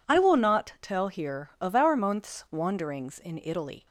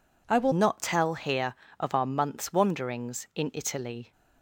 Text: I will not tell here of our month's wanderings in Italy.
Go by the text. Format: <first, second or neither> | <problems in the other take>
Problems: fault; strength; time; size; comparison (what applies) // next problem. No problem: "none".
first | changes voice at "not"; from 0.5 s on; 3.6 s long